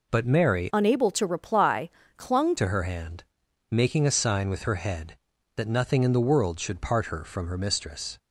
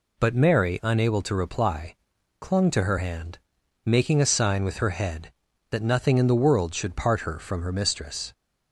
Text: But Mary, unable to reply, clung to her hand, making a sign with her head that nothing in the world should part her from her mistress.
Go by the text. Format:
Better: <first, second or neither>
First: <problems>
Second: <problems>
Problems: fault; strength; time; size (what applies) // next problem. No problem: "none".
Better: second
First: changes voice from "unable" to "clung"; from 0.7 to 2.5 s; 1.8 s long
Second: none